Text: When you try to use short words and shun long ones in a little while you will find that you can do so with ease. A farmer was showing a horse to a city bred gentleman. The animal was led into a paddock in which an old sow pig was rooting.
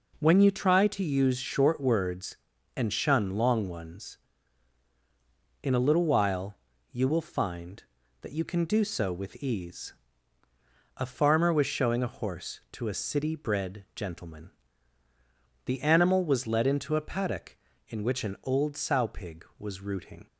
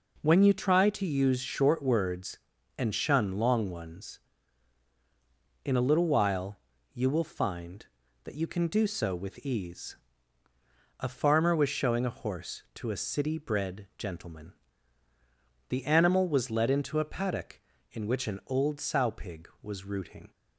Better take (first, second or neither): neither